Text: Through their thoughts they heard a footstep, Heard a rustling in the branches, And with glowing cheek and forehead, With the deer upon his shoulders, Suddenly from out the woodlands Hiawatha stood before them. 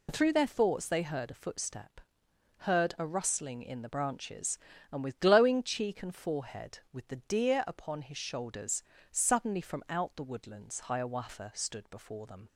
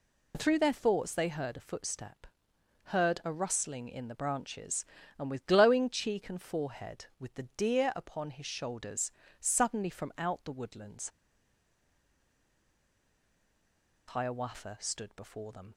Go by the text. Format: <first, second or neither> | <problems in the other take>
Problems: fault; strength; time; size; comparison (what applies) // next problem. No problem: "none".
first | pauses between "woodlands" and "Hiawatha"; strong; at 11.0 s; 2.9 s long